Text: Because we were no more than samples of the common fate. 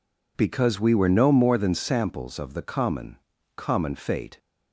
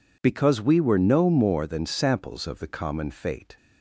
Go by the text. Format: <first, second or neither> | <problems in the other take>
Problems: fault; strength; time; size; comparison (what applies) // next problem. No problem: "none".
second | says "common" twice; at 3.5 s